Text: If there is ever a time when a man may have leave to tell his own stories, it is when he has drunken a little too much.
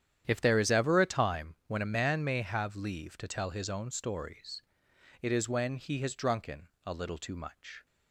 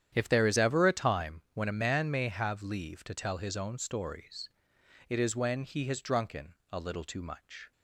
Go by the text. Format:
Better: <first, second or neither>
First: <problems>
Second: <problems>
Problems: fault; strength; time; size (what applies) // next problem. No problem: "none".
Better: neither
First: starts louder than the rest; strong; until 1.2 s; 10 dB // pauses between "drunken" and "a"; slight; at 6.6 s; 0.18 s long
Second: starts louder than the rest; strong; until 1.1 s; 9.5 dB // pauses between "drunken" and "a"; slight; at 6.5 s; 0.18 s long